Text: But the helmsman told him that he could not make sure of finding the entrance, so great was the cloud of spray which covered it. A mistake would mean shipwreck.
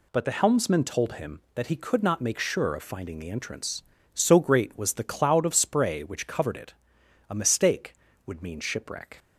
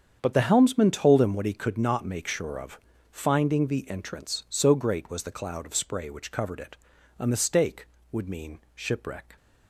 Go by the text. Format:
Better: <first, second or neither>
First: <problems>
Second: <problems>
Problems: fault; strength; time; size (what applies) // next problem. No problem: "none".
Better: first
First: none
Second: starts louder than the rest; strong; until 1.2 s; 8 dB // says "what" for "that"; at 1.3 s // pauses between "of" and "finding"; slight; at 2.7 s; 0.32 s long // pauses between "mean" and "shipwreck"; slight; at 8.5 s; 0.16 s long